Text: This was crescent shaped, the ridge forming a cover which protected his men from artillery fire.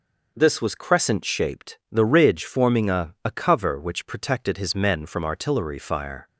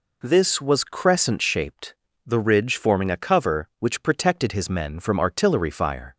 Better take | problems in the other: second | says "a" twice; at 3.2 s

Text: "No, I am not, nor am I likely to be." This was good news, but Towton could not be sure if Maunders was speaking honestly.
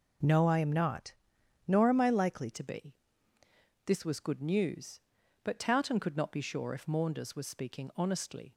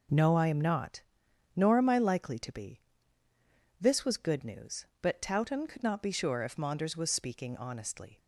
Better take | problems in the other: second | changes voice at "to"; from 2.5 s on; 6.0 s long

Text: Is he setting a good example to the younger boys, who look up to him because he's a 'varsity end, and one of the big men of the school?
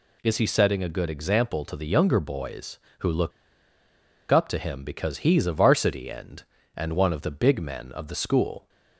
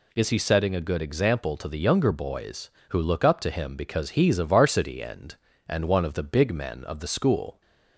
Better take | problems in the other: second | pauses between "look" and "up"; at 3.3 s; 0.99 s long

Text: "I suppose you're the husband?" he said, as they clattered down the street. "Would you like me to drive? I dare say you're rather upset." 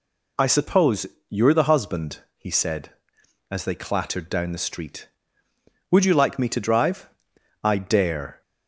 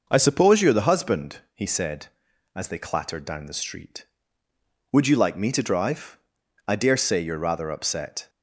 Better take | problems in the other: second | pauses between "suppose" and "you're"; slight; at 1.0 s; 0.24 s long // stops before "say you're rather upset"; at 8.4 s

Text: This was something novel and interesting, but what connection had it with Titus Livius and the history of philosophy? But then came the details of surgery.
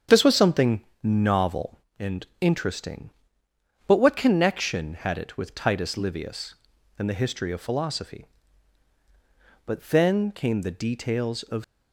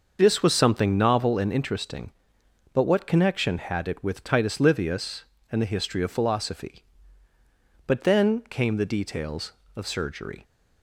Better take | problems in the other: second | starts louder than the rest; strong; until 1.3 s; 7.5 dB; also in the second // pauses between "something" and "novel"; slight; at 0.8 s; 0.20 s long // stops before "surgery"; at 11.6 s

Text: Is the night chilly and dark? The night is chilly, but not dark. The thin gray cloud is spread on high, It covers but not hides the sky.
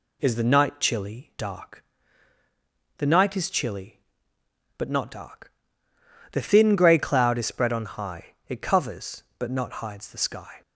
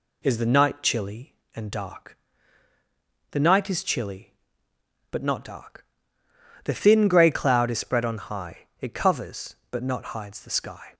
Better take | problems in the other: second | skips "and"; at 1.3 s

